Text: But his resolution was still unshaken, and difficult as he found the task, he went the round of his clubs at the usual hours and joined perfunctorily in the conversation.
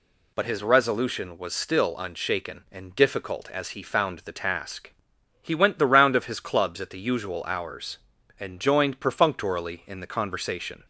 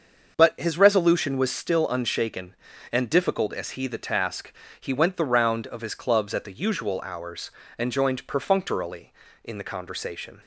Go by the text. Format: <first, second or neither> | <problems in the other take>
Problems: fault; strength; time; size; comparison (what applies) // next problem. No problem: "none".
first | starts louder than the rest; until 1.3 s; 6.5 dB // skips "found"; at 3.8 s